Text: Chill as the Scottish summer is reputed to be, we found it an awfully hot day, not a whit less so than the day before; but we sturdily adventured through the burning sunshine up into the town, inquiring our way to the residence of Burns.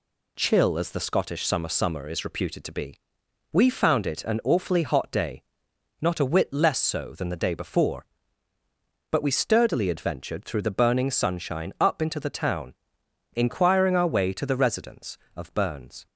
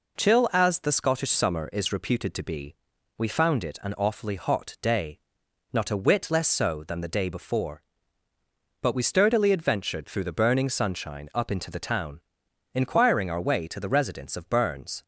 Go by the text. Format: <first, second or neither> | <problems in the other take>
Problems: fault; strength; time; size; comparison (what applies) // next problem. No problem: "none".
second | says "summer" twice; at 1.6 s